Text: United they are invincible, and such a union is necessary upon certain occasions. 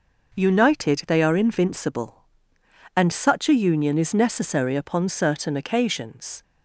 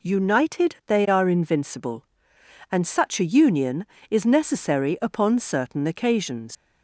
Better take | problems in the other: first | leaves "occasions" unfinished; at 6.5 s; 90 ms

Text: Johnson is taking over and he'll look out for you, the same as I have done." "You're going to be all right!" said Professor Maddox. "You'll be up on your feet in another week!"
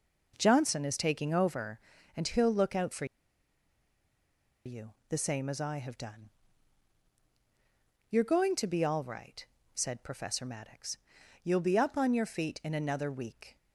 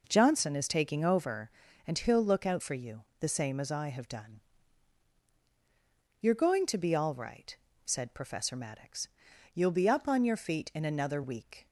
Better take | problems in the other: second | pauses between "for" and "you"; strong; at 3.0 s; 1.6 s long

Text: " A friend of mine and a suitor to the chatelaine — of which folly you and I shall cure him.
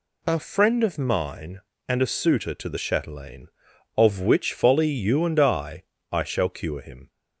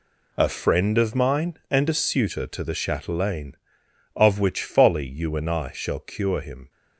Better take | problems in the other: second | says "I" twice; at 6.1 s

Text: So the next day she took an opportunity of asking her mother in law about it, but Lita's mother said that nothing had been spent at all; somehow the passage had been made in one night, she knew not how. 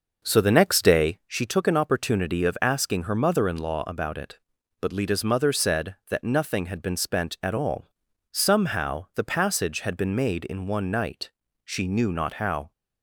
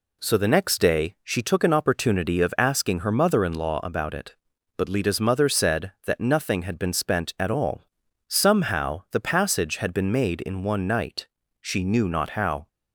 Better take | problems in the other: second | starts louder than the rest; noticeable; until 1.3 s; 5.5 dB

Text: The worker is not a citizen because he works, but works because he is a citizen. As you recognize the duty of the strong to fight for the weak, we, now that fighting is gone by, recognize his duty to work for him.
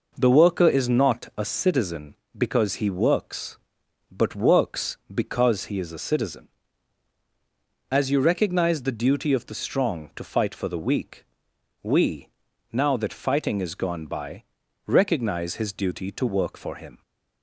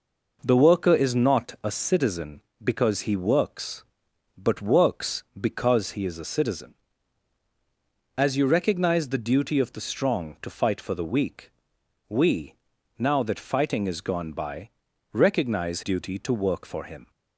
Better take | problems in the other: first | skips "his"; at 15.8 s

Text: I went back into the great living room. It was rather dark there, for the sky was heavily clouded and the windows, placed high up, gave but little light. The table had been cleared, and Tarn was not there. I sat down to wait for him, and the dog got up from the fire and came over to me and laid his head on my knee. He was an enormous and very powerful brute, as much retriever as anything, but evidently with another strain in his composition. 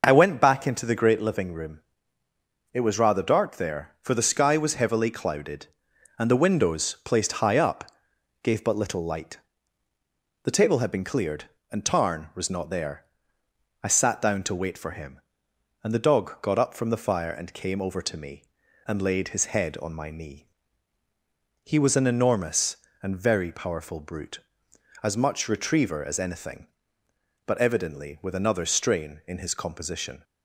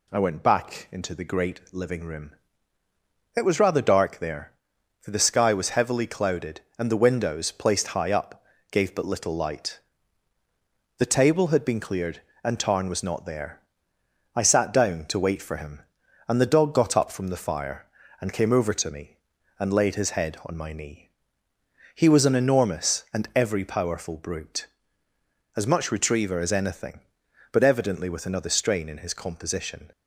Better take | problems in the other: first | says "every" for "very"; at 23.3 s

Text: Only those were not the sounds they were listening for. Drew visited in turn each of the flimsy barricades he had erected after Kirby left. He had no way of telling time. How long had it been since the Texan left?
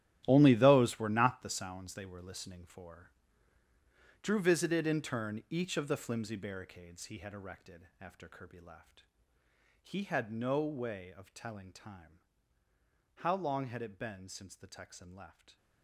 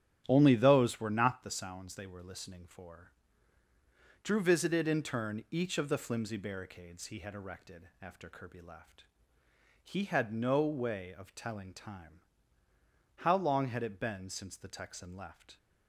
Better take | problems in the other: second | gets quieter; strong; throughout; 14.5 dB // starts louder than the rest; strong; until 1.2 s; 12.5 dB; strong in the second

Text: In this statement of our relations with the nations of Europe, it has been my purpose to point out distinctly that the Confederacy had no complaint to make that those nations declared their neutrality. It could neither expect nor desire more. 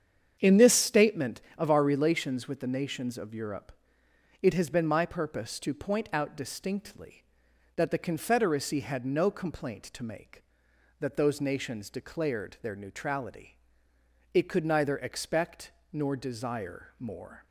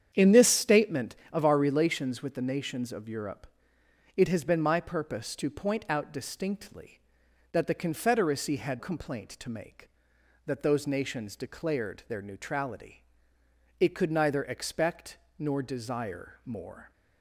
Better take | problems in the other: first | starts louder than the rest; strong; until 1.1 s; 8.5 dB; strong in the first // skips "no"; at 8.7 s // pauses between "expect" and "nor"; slight; at 15.1 s; 0.18 s long; slight in the first

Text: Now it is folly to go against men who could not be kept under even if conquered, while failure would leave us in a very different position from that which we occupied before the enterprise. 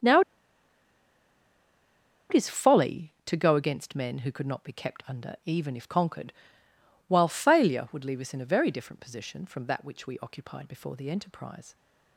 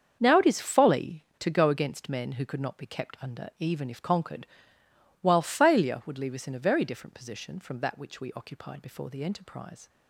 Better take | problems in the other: second | starts louder than the rest; until 3.1 s; 7 dB; also in the second // pauses between "Now" and "it"; strong; at 0.2 s; 2.0 s long

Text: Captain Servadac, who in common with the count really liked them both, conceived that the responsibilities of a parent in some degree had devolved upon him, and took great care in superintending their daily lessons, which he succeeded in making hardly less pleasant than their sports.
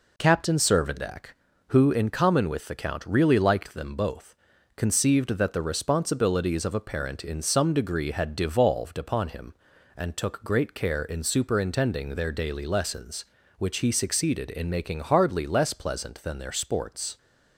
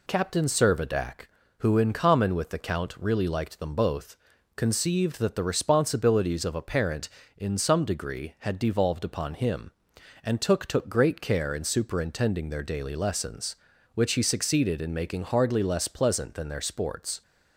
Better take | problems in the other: first | says "took" twice; at 10.6 s

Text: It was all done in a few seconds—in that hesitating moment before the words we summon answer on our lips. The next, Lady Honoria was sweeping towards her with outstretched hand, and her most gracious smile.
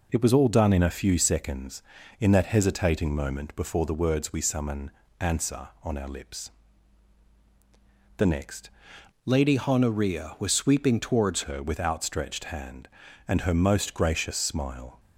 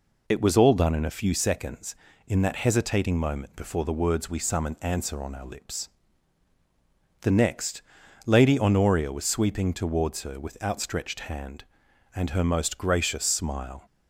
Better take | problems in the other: second | pauses between "summon" and "answer"; slight; at 4.9 s; 0.30 s long // changes voice from "Lady" to "towards"; from 9.2 to 11.4 s; 2.2 s long

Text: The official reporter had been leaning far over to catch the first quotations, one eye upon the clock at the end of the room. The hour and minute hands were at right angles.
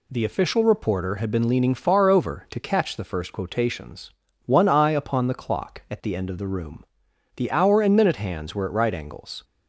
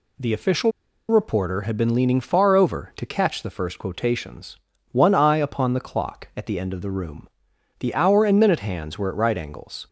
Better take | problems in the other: first | pauses between "official" and "reporter"; at 0.7 s; 0.40 s long

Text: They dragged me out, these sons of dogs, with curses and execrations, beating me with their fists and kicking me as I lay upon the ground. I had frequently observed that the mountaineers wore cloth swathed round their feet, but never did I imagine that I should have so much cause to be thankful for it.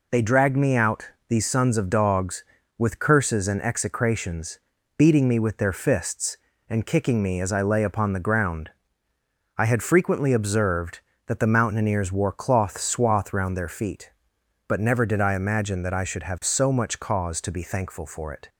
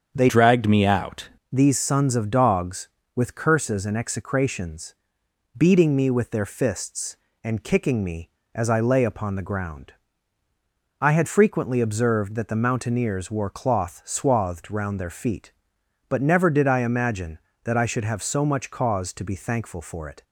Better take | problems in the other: first | starts louder than the rest; strong; until 1.1 s; 7 dB // changes voice from "dragged" to "out"; from 0.2 to 1.2 s; 1.0 s long

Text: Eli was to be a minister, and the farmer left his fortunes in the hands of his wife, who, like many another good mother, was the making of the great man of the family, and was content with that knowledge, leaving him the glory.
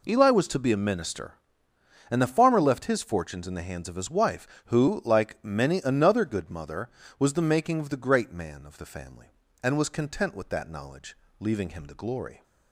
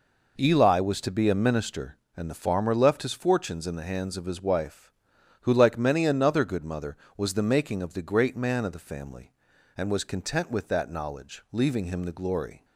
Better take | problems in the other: neither | none

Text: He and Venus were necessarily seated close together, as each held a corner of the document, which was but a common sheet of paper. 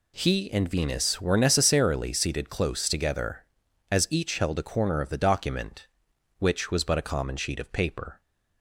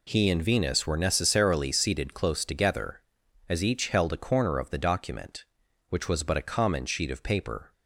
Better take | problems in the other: neither | none

